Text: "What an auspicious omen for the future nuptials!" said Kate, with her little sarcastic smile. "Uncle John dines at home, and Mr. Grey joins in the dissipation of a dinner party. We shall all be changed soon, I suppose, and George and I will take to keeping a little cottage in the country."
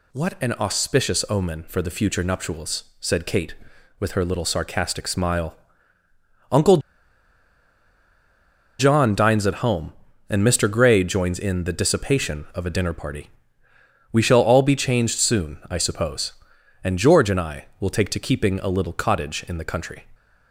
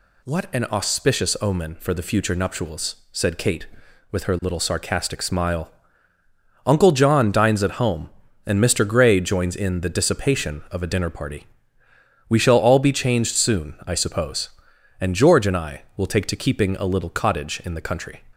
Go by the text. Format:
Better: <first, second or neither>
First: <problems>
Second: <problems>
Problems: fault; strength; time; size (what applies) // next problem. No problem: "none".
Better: second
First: pauses between "Uncle" and "John"; strong; at 6.7 s; 2.0 s long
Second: none